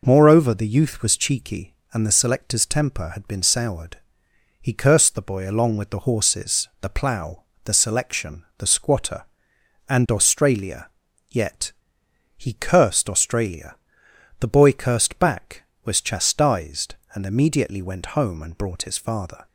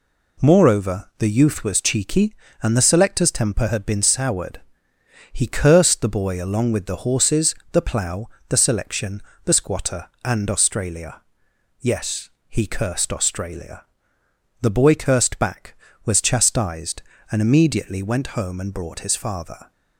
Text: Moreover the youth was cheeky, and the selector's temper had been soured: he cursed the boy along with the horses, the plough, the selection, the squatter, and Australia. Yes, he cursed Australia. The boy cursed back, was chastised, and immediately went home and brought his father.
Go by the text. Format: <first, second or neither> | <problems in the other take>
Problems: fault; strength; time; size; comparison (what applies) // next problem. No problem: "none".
second | says "Yet" for "Yes"; at 11.2 s